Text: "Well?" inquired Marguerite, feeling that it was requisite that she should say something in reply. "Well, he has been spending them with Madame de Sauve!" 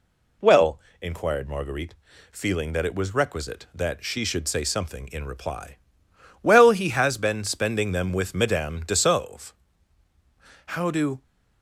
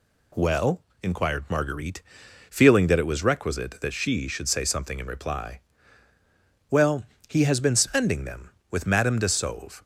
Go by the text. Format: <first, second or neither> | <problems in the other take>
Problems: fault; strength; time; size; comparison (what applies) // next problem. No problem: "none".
second | goes on to say "How do"; from 10.6 s on; 0.56 s long